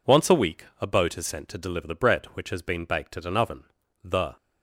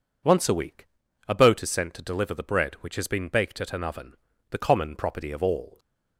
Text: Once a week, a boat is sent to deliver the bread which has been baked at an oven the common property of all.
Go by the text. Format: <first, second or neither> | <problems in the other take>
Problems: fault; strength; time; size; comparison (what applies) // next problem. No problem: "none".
second | pauses between "oven" and "the"; at 3.6 s; 0.40 s long; also in the second // stops before "common property of all"; at 4.3 s